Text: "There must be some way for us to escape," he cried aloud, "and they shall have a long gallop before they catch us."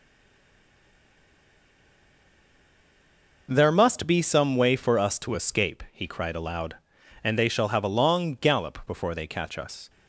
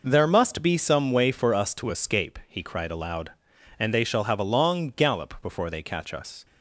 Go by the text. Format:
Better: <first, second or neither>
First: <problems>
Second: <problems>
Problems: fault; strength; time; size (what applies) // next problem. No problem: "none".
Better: second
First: stays silent before the first word; strong; until 3.4 s; 3.4 s long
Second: none